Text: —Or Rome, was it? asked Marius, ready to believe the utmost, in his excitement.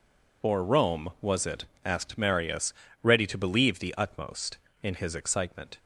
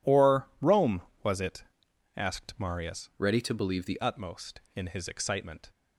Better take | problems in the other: first | changes voice from "ready" to "the"; from 3.1 to 3.9 s; 0.8 s long

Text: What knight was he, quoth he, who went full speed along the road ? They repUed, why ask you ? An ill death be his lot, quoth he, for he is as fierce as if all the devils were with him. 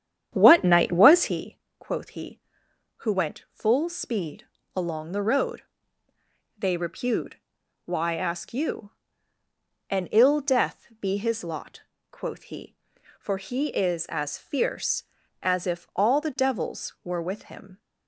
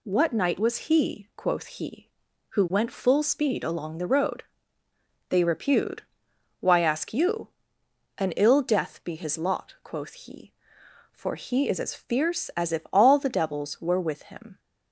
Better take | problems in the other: second | starts louder than the rest; strong; until 1.4 s; 9 dB // pauses between "speed" and "along"; slight; at 4.4 s; 0.30 s long

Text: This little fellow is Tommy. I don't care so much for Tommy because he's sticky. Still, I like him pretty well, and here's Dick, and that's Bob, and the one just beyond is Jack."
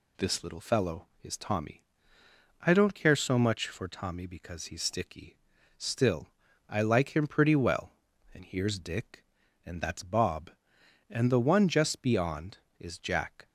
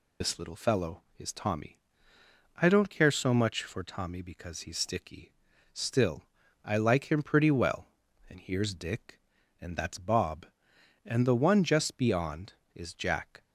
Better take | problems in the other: first | loses the start of "This"; at 0.2 s; 80 ms

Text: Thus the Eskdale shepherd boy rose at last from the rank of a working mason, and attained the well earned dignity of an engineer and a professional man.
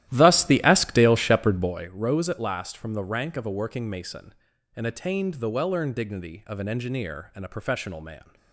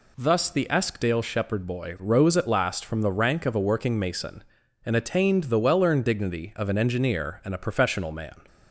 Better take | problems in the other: second | starts louder than the rest; strong; until 1.9 s; 13.5 dB

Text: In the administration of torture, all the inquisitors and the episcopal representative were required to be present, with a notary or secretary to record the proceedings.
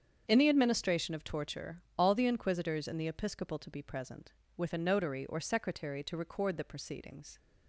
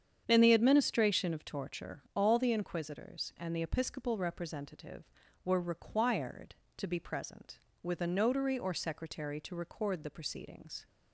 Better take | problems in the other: second | starts louder than the rest; strong; until 1.2 s; 7.5 dB; strong in the second // skips "representative were required"; at 3.6 s

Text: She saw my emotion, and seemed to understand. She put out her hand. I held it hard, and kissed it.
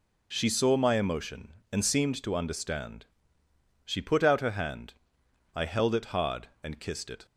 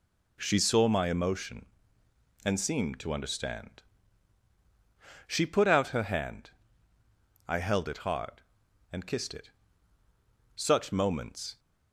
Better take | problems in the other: first | goes on to say "Such moments"; noticeable; from 10.5 s on; 1.0 s long

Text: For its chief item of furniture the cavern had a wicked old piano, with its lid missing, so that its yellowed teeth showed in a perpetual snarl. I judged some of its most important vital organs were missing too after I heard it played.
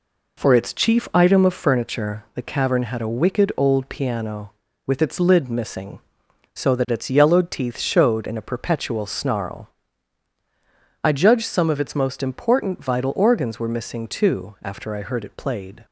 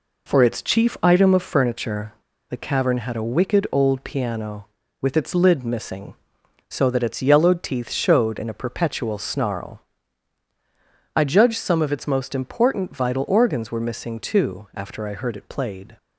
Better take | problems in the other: first | pauses between "furniture" and "the"; at 2.1 s; 0.38 s long

